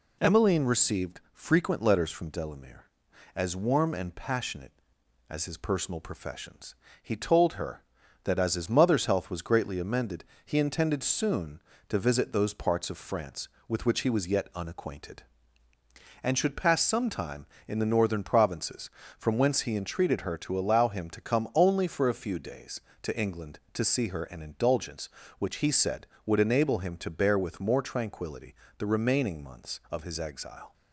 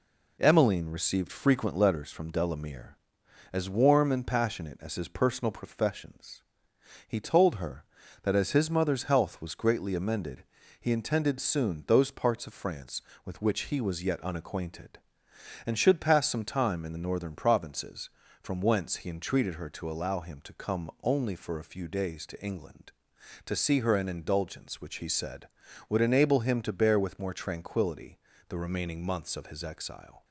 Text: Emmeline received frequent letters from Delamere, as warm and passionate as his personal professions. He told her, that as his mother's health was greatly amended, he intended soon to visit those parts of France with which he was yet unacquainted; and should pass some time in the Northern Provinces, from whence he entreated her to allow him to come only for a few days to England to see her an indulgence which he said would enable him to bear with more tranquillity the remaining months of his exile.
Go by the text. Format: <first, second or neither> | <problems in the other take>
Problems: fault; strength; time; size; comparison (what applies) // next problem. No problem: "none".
first | skips "to visit"; at 11.8 s // pauses between "tranquillity" and "the"; slight; at 28.1 s; 0.30 s long; slight in the first